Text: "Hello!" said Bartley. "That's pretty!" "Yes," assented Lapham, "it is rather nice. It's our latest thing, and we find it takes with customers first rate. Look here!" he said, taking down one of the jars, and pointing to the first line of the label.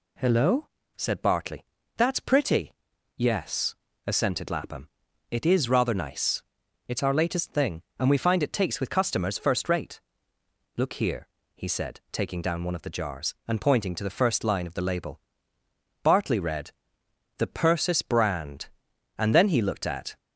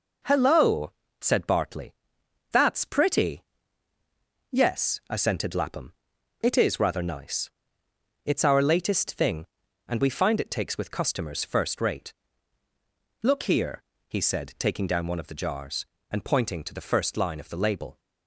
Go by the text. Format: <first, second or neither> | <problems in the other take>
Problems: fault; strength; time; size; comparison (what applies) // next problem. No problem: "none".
second | goes on to say "Bartley read THE PERSIS BRAND and then he looked at"; strong; from 16.0 s on; 4.1 s long